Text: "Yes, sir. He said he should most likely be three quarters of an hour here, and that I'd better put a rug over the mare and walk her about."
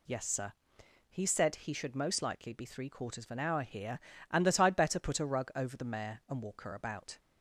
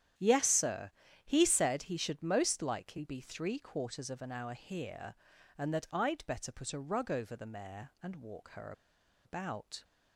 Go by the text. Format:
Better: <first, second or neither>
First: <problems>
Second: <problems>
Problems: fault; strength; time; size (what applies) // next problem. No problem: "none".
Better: first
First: none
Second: starts louder than the rest; strong; until 1.5 s; 10 dB // pauses between "her" and "about"; noticeable; at 8.7 s; 0.53 s long